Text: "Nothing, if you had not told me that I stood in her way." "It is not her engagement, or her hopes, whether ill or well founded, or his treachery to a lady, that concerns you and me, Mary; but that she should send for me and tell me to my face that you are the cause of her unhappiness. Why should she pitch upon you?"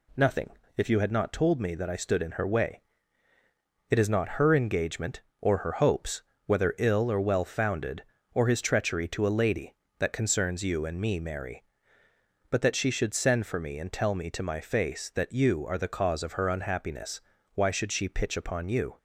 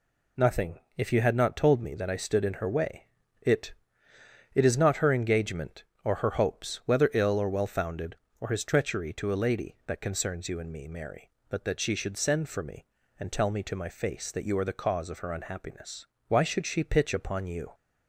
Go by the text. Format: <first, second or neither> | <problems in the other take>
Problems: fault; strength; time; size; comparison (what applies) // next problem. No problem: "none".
first | says "It" twice; at 4.5 s